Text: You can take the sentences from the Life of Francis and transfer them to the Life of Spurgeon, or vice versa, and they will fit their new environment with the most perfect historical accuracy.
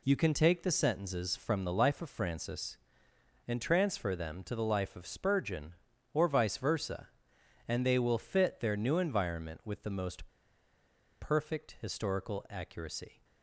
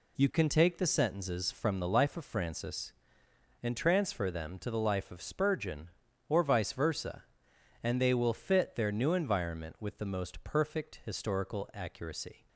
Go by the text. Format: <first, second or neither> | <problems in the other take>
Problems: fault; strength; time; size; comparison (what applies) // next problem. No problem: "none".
second | pauses between "most" and "perfect"; noticeable; at 10.2 s; 0.94 s long